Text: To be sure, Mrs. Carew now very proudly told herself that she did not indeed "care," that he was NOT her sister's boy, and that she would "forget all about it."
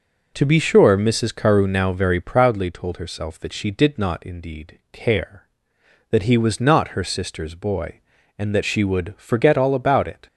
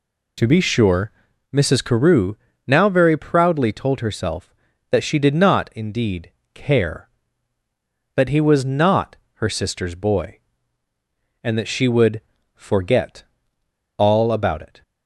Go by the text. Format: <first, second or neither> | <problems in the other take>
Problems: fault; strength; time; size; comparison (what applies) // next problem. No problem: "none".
first | pauses between "Carew" and "now"; slight; at 2.3 s; 0.30 s long // pauses between "indeed" and "care"; slight; at 6.3 s; 0.22 s long // pauses between "NOT" and "her"; slight; at 9.1 s; 0.26 s long // pauses between "would" and "forget"; slight; at 12.2 s; 0.34 s long // pauses between "forget" and "all"; noticeable; at 13.2 s; 0.73 s long